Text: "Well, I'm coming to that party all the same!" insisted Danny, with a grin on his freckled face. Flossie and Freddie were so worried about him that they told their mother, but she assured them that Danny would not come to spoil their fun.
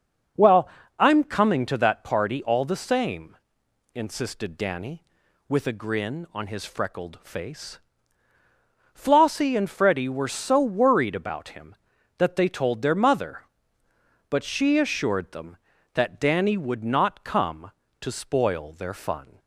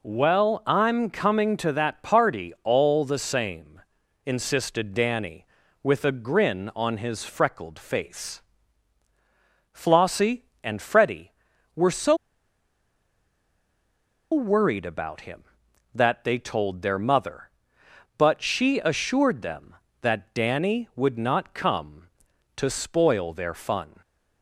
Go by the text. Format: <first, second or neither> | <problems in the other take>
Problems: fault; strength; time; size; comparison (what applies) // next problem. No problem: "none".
first | pauses between "so" and "worried"; strong; at 12.1 s; 2.1 s long